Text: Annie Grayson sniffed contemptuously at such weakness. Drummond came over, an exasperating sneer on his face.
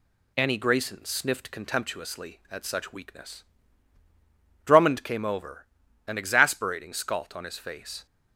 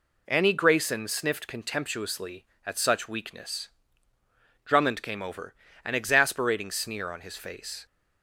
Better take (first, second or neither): second